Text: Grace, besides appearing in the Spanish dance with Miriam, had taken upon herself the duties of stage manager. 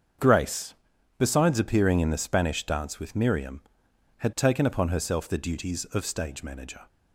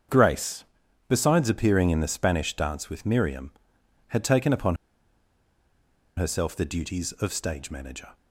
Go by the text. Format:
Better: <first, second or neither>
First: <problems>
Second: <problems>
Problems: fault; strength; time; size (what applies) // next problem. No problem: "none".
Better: first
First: starts louder than the rest; until 1.6 s; 7 dB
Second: starts louder than the rest; until 1.5 s; 7 dB // pauses between "upon" and "herself"; strong; at 4.7 s; 1.4 s long